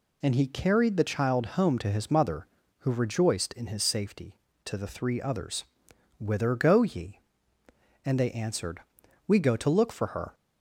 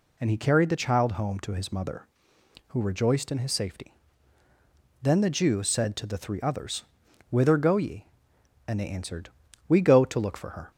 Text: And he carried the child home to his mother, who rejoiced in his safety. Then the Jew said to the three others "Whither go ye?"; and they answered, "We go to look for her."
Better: second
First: skips "Then the Jew said"; at 4.5 s // pauses between "others" and "Whither"; noticeable; at 5.6 s; 0.54 s long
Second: pauses between "others" and "Whither"; noticeable; at 6.8 s; 0.46 s long

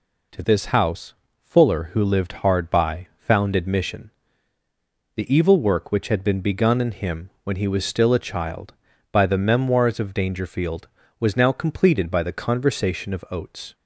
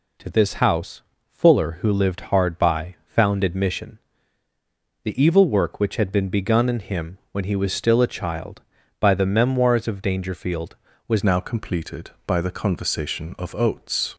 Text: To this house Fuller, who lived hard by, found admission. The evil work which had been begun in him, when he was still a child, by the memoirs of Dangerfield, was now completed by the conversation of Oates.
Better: first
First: pauses between "house" and "Fuller"; slight; at 1.1 s; 0.28 s long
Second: pauses between "house" and "Fuller"; slight; at 1.0 s; 0.28 s long // changes voice at "now"; from 11.2 s on; 2.9 s long

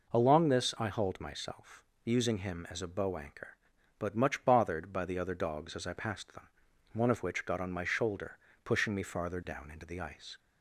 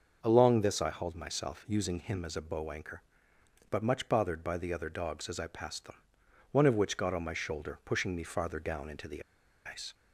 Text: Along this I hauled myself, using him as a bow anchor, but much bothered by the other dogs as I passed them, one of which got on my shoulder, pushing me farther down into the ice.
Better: first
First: none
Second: starts louder than the rest; until 1.2 s; 6.5 dB // pauses between "the" and "ice"; at 9.2 s; 0.43 s long

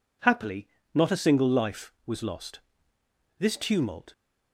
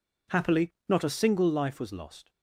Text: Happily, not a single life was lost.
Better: second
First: goes on to say "This tumult"; noticeable; from 3.3 s on; 0.74 s long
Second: none

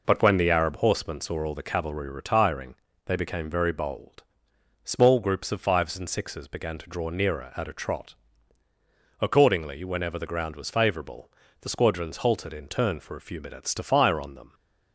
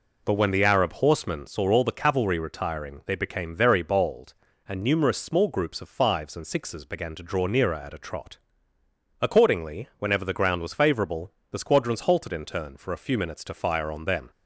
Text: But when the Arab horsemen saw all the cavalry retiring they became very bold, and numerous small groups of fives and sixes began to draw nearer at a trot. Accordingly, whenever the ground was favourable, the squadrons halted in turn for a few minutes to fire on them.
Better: second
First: pauses between "retiring" and "they"; slight; at 2.7 s; 0.30 s long // skips "and numerous"; at 4.5 s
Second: none

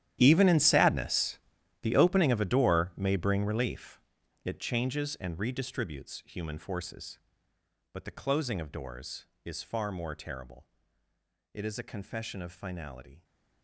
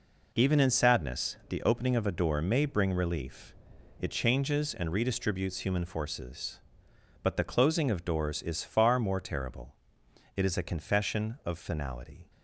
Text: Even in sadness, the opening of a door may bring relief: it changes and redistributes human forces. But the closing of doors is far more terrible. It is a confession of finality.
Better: second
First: gets quieter; strong; throughout; 16.5 dB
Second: none

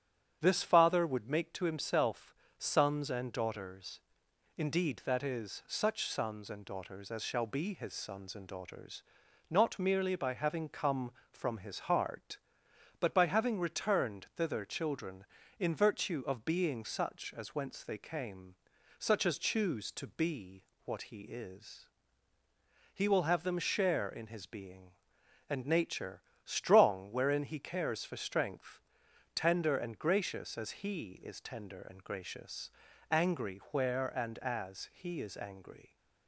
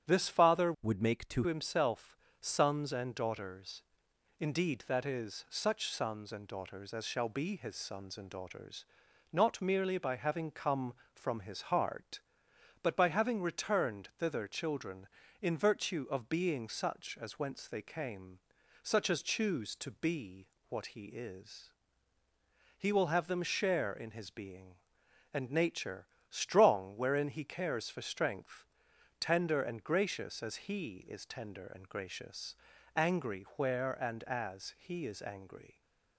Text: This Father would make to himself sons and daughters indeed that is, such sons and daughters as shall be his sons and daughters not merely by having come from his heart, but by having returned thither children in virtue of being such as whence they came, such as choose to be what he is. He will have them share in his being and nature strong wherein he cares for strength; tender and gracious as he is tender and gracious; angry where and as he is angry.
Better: first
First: starts louder than the rest; strong; until 1.4 s; 8.5 dB // pauses between "himself" and "sons"; slight; at 2.3 s; 0.24 s long // pauses between "daughters" and "indeed"; noticeable; at 4.0 s; 0.58 s long // pauses between "daughters" and "not"; noticeable; at 9.0 s; 0.46 s long // pauses between "be" and "what"; slight; at 20.6 s; 0.22 s long // pauses between "nature" and "strong"; slight; at 26.2 s; 0.22 s long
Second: starts louder than the rest; strong; until 1.1 s; 8.5 dB // changes voice from "would" to "to"; from 0.8 to 1.4 s; 0.6 s long // pauses between "himself" and "sons"; slight; at 2.1 s; 0.24 s long // pauses between "daughters" and "indeed"; noticeable; at 3.8 s; 0.58 s long // pauses between "daughters" and "not"; noticeable; at 8.8 s; 0.46 s long // pauses between "be" and "what"; slight; at 20.4 s; 0.22 s long // pauses between "nature" and "strong"; slight; at 26.0 s; 0.22 s long

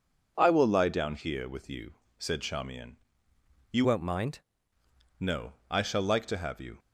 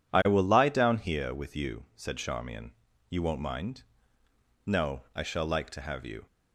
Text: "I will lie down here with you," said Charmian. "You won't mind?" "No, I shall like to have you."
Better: second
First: changes voice from "won't" to "mind"; from 3.8 to 4.3 s; 0.5 s long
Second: none

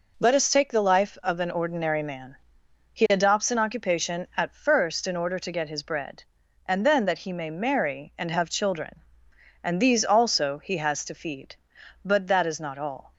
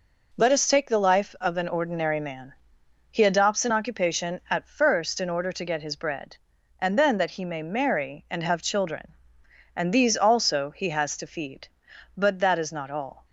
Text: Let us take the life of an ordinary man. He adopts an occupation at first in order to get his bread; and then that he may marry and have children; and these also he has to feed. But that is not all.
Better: neither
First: none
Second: none

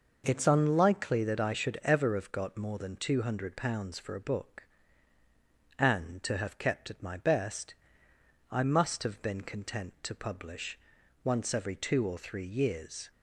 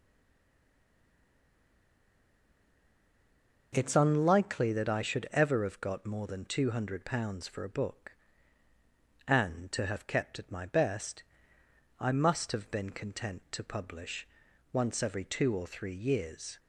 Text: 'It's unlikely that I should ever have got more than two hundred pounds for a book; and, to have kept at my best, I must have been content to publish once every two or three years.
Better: first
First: pauses between "publish" and "once"; at 10.7 s; 0.44 s long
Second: stays silent before the first word; strong; until 3.7 s; 3.7 s long // pauses between "publish" and "once"; at 14.2 s; 0.44 s long

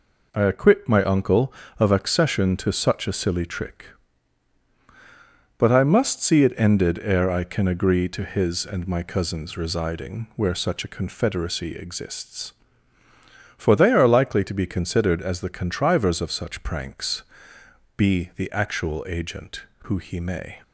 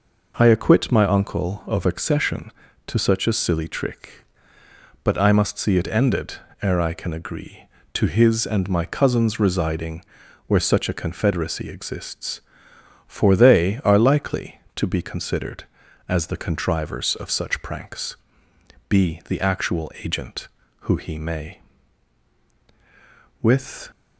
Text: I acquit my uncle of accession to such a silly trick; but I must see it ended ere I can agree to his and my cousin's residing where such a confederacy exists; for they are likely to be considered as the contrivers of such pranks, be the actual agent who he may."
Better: first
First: none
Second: pauses between "ended" and "ere"; slight; at 6.3 s; 0.28 s long // pauses between "residing" and "where"; at 10.0 s; 0.44 s long // goes on to say "With"; slight; from 23.4 s on; 0.48 s long

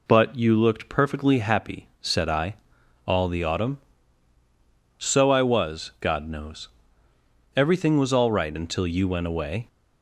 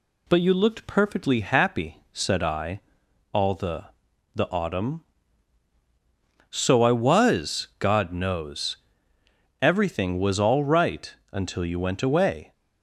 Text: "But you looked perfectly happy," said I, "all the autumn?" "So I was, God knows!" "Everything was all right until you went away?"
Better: first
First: none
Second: says "the" twice; at 4.3 s // pauses between "right" and "until"; slight; at 11.1 s; 0.16 s long

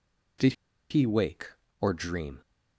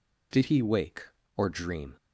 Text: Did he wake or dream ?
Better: second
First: pauses between "Did" and "he"; at 0.5 s; 0.36 s long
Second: none

